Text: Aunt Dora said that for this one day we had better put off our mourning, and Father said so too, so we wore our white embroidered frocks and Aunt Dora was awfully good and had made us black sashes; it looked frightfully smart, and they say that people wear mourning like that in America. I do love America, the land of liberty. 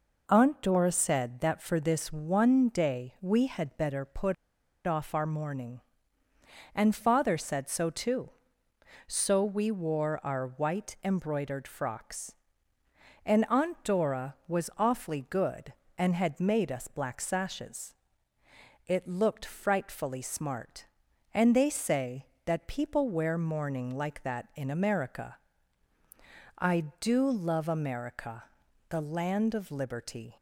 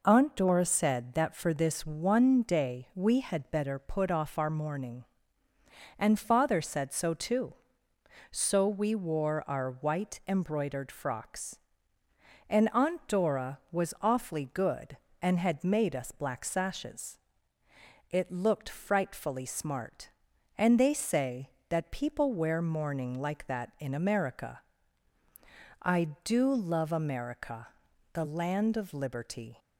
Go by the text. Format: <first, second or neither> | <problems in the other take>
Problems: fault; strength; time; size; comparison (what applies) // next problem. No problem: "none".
second | pauses between "put" and "off"; noticeable; at 4.3 s; 0.51 s long